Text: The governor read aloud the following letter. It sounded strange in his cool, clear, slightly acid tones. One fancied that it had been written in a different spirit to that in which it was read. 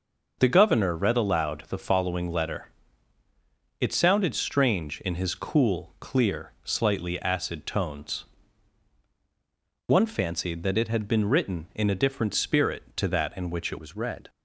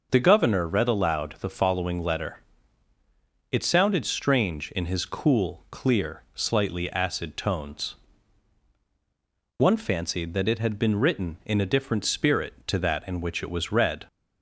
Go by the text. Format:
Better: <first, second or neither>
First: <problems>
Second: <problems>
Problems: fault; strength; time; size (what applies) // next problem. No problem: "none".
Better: second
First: changes voice at "was"; from 13.7 s on; 0.5 s long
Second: none